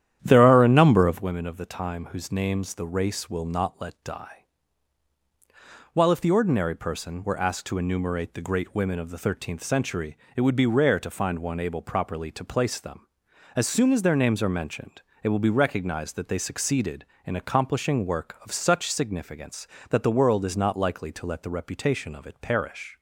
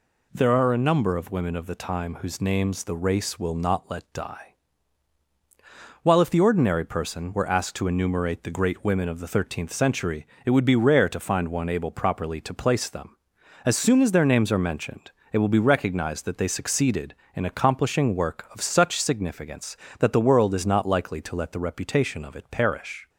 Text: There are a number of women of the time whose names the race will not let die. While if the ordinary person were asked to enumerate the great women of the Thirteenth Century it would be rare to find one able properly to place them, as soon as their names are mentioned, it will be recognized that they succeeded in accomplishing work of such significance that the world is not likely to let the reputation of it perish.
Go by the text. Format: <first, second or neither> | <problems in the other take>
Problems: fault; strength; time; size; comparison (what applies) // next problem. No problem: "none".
second | starts louder than the rest; strong; until 1.3 s; 10.5 dB // pauses between "Century" and "it"; slight; at 10.1 s; 0.18 s long; slight in the second